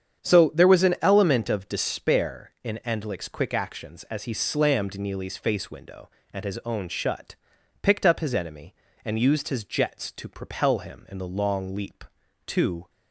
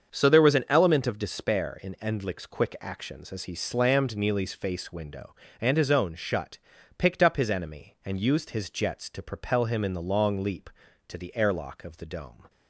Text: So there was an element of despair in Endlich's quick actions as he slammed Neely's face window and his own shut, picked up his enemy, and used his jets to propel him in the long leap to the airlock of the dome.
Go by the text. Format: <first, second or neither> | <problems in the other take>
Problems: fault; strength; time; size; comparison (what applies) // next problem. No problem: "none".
second | starts louder than the rest; strong; until 1.3 s; 8 dB; also in the second // stops before "the airlock of the dome"; at 12.8 s